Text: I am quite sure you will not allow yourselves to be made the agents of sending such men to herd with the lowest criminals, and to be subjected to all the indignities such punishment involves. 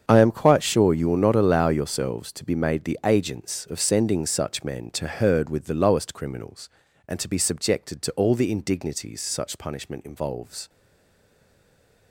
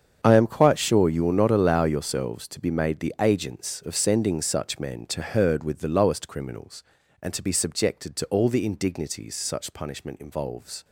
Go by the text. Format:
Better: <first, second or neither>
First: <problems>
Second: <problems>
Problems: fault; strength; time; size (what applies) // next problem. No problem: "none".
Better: second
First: starts louder than the rest; strong; until 1.0 s; 7.5 dB // stays silent after the last word; noticeable; from 10.6 s on; 1.5 s long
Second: starts louder than the rest; strong; until 1.2 s; 7.5 dB